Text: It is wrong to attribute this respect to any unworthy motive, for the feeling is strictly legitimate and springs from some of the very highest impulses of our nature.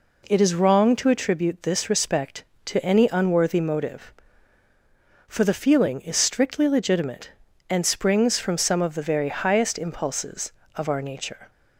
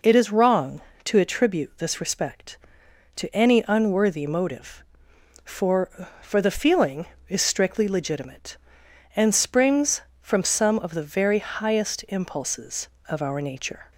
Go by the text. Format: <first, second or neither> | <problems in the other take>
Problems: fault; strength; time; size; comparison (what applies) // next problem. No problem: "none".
first | says "for" twice; at 6.2 s